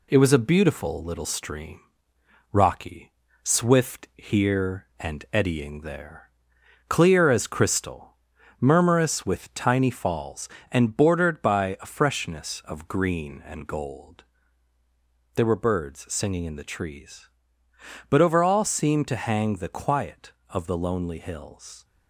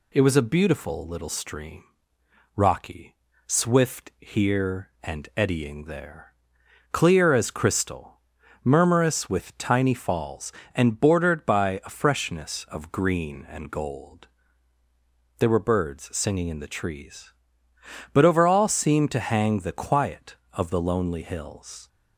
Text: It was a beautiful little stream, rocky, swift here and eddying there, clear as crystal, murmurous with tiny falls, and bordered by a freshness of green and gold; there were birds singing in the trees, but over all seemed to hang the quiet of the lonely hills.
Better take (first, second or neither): second